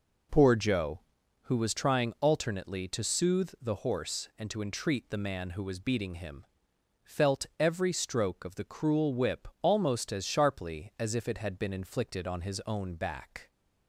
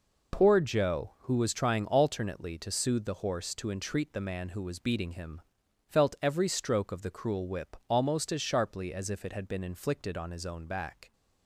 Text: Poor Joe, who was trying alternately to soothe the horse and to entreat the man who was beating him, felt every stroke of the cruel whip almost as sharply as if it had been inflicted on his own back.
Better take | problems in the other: first | skips "and"; at 3.5 s

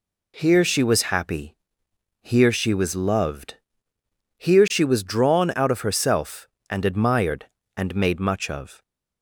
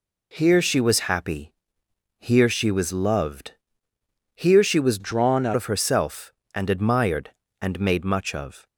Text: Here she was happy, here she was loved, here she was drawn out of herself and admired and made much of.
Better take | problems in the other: first | changes voice from "drawn" to "out"; from 4.9 to 5.5 s; 0.6 s long

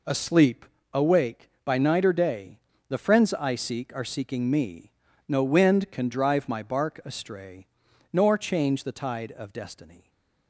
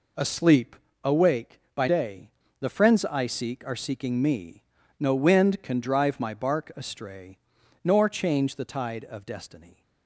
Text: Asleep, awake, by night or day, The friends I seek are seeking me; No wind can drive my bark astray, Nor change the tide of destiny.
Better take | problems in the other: first | skips "night or"; at 1.8 s

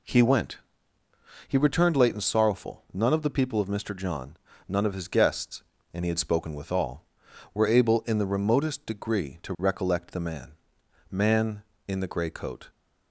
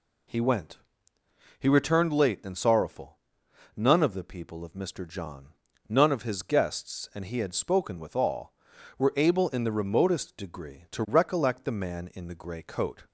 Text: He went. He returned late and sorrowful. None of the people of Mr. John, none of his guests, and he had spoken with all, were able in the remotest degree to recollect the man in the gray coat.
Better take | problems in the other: second | says "man" twice; at 11.1 s

